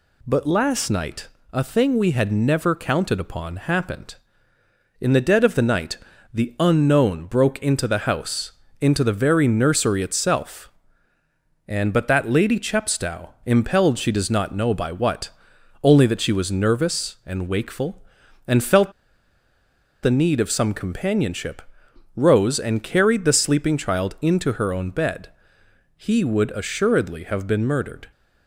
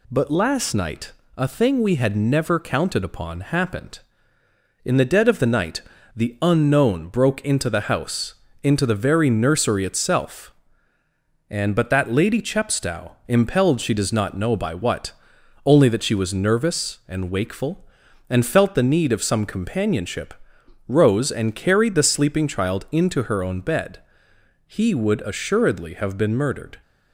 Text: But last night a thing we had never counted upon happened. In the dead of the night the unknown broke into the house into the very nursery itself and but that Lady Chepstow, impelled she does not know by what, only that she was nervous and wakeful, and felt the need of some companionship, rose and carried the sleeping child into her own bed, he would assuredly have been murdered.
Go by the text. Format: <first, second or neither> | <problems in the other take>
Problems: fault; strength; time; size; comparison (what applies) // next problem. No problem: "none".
second | pauses between "night" and "a"; slight; at 1.2 s; 0.26 s long; slight in the second // pauses between "night" and "the"; slight; at 5.9 s; 0.36 s long; slight in the second // pauses between "house" and "into"; slight; at 8.5 s; 0.28 s long; slight in the second // pauses between "felt" and "the"; at 18.9 s; 1.1 s long